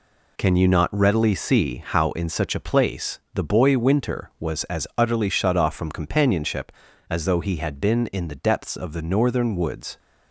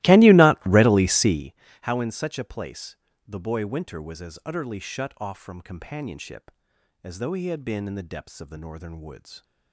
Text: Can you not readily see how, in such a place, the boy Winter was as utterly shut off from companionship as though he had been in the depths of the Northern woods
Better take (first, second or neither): first